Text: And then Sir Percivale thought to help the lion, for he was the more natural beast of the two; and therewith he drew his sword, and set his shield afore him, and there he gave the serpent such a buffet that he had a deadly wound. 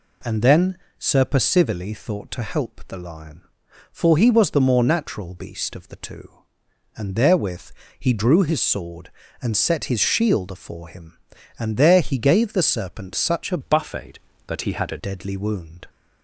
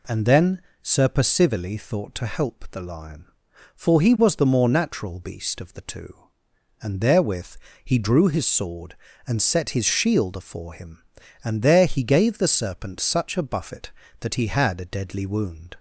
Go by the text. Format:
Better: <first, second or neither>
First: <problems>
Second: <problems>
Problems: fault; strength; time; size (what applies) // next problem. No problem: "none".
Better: second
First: pauses between "then" and "Sir"; slight; at 0.7 s; 0.20 s long // pauses between "therewith" and "he"; slight; at 7.7 s; 0.26 s long // changes voice from "buffet" to "a"; from 13.6 to 14.9 s; 1.3 s long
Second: pauses between "then" and "Sir"; slight; at 0.6 s; 0.20 s long // pauses between "therewith" and "he"; slight; at 7.5 s; 0.26 s long